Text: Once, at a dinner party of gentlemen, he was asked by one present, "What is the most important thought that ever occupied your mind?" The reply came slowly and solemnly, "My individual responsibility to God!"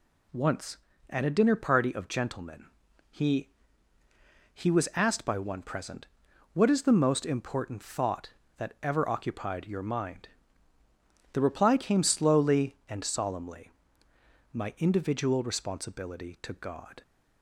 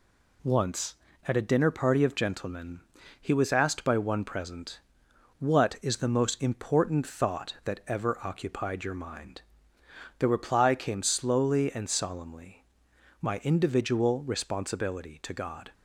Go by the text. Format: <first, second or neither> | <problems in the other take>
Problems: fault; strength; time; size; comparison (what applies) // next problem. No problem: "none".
second | says "he" twice; at 4.5 s